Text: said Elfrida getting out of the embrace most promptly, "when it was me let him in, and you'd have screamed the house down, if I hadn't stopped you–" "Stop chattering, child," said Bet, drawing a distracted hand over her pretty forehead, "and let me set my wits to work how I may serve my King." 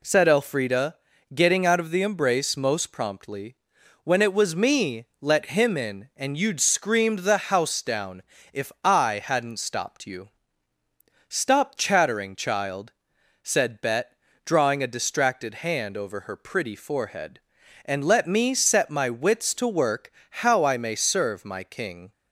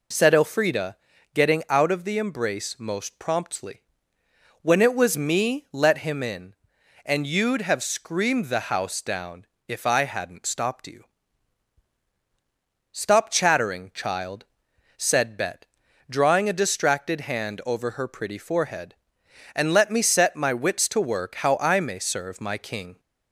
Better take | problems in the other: second | pauses between "Elfrida" and "getting"; at 0.9 s; 0.38 s long; also in the second // skips "have"; at 6.6 s // pauses between "work" and "how"; slight; at 20.1 s; 0.18 s long

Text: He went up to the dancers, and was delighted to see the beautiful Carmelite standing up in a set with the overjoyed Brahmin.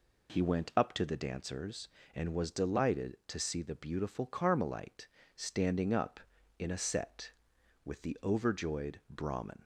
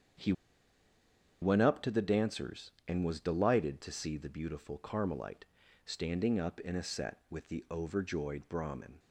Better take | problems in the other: first | starts louder than the rest; strong; until 2.3 s; 8 dB // pauses between "He" and "went"; at 0.3 s; 1.0 s long // pauses between "Carmelite" and "standing"; at 5.4 s; 0.38 s long; slight in the first

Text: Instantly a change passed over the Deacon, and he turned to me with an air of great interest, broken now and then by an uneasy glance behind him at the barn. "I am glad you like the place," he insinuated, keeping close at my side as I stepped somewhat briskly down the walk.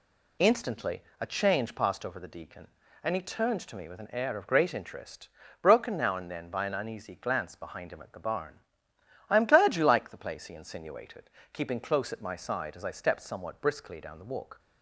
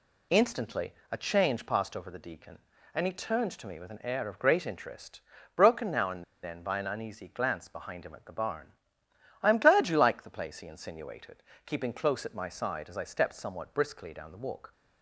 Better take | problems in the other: first | pauses between "Instantly" and "a"; slight; at 0.9 s; 0.20 s long; slight in the first // pauses between "and" and "then"; slight; at 6.2 s; 0.19 s long

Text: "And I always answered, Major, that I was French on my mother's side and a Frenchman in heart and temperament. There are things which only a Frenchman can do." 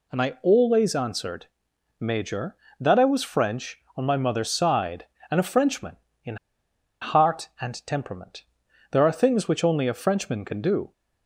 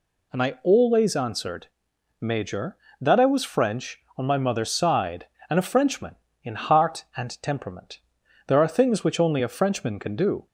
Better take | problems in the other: second | pauses between "in" and "heart"; noticeable; at 6.3 s; 0.65 s long

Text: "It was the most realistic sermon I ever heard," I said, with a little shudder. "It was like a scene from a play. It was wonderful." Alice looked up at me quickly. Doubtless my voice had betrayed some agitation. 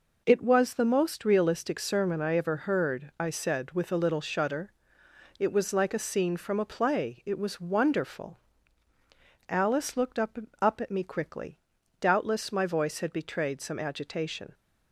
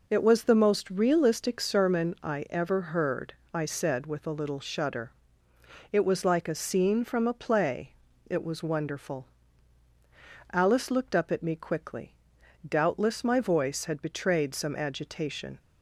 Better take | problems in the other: second | says "up" twice; at 10.6 s

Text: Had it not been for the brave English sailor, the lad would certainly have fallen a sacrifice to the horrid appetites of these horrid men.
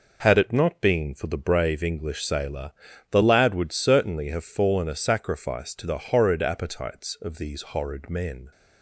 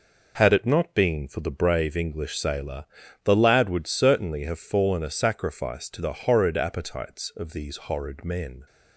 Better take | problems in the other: neither | none

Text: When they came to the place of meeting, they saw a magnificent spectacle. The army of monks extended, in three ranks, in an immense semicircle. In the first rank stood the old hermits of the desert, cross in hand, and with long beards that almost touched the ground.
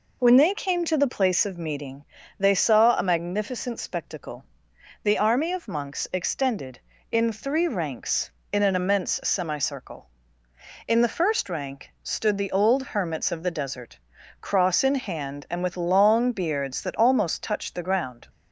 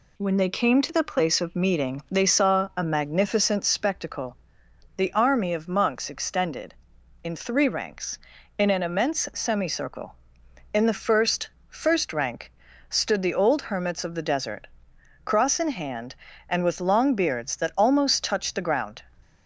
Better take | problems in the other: first | says "first" twice; at 11.6 s // pauses between "rank" and "stood"; at 12.4 s; 0.38 s long

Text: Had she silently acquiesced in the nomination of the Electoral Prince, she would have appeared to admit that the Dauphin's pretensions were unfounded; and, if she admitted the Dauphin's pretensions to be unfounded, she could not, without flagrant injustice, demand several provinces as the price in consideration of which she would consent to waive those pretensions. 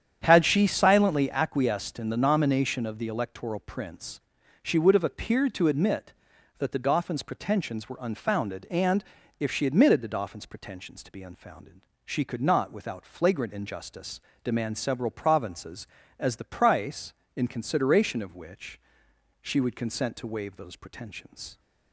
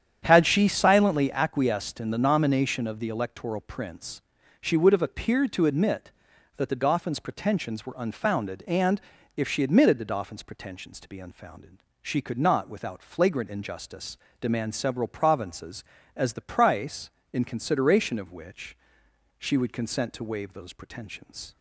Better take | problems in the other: neither | starts louder than the rest; strong; the same in both // pauses between "which" and "she"; noticeable; the same in both

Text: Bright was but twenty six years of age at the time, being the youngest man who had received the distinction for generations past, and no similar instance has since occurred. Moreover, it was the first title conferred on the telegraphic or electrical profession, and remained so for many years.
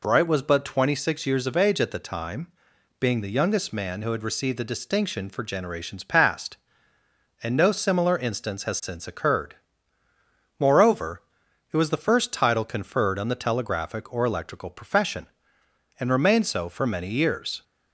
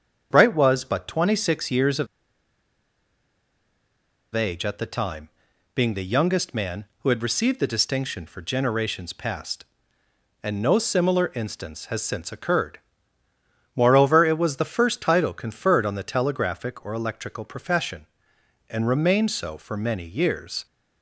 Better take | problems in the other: first | starts louder than the rest; strong; until 1.3 s; 7.5 dB // pauses between "of" and "age"; strong; at 2.0 s; 2.2 s long

